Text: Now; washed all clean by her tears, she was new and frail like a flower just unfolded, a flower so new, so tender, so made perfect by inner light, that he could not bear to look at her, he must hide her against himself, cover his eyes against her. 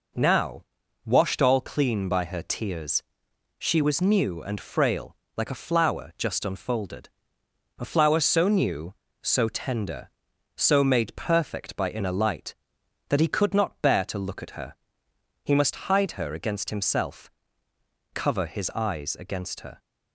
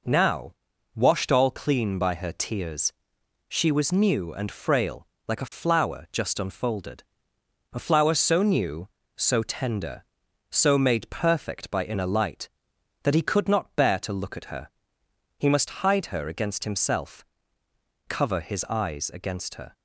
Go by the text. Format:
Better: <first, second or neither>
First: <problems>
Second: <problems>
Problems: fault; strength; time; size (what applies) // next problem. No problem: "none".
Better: neither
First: pauses between "frail" and "like"; slight; at 5.1 s; 0.22 s long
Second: pauses between "frail" and "like"; slight; at 5.0 s; 0.22 s long